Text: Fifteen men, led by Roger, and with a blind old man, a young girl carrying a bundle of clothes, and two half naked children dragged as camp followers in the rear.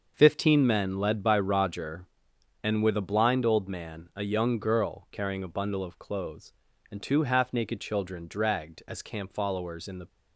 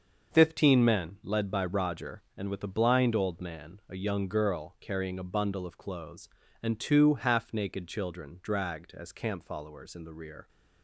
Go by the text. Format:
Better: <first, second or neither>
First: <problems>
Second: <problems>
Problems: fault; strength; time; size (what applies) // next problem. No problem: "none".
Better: second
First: starts louder than the rest; until 1.1 s; 6.5 dB // stops before "rear"; at 10.0 s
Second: starts louder than the rest; until 1.3 s; 6.5 dB